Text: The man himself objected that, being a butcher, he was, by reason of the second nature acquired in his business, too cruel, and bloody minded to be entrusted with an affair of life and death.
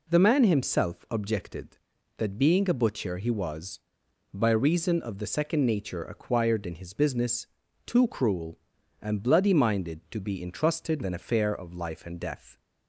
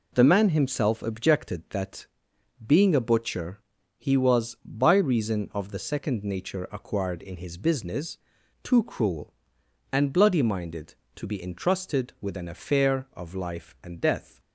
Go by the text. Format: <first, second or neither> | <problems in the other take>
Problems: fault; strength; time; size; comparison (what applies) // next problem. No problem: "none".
second | skips "with"; at 11.0 s